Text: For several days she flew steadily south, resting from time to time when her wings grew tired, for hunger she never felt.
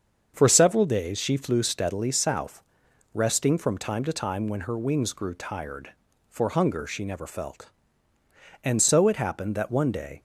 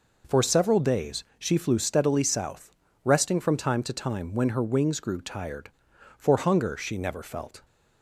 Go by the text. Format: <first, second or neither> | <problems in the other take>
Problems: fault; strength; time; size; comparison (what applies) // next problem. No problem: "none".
second | starts louder than the rest; until 1.3 s; 7 dB // goes on to say "And so it happened that one day"; from 8.6 s on; 1.6 s long